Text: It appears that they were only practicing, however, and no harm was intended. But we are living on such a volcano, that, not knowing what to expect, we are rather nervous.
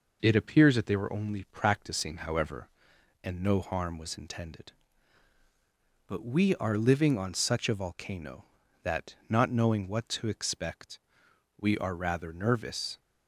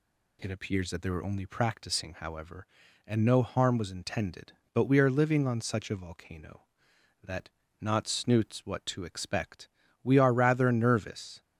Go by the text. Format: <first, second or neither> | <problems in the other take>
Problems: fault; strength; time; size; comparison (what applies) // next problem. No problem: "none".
first | says "snoots" for "knowing"; at 8.0 s